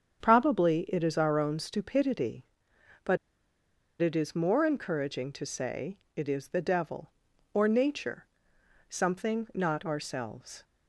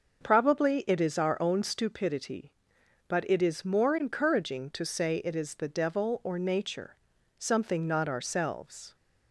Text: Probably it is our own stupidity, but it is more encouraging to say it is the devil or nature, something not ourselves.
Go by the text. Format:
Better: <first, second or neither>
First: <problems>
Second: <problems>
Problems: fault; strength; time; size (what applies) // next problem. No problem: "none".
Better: second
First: starts louder than the rest; strong; until 1.2 s; 7.5 dB // pauses between "but" and "it"; noticeable; at 3.1 s; 0.83 s long // pauses between "say" and "it"; slight; at 5.9 s; 0.18 s long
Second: starts louder than the rest; until 1.2 s; 6 dB